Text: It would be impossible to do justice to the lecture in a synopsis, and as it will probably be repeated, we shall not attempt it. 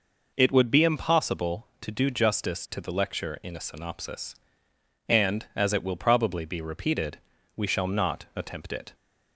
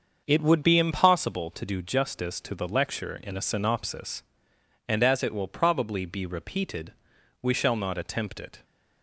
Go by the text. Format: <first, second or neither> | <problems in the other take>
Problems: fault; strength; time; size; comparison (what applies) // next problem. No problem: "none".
first | starts louder than the rest; until 1.2 s; 6.5 dB